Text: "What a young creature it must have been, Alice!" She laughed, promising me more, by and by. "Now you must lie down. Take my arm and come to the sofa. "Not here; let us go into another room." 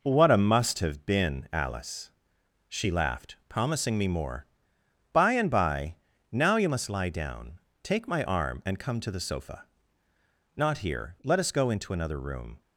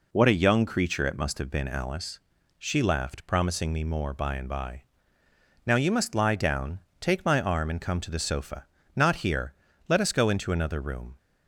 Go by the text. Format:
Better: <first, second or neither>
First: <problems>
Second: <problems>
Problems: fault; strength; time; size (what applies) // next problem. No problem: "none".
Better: second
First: skips "young creature it"; at 0.3 s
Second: none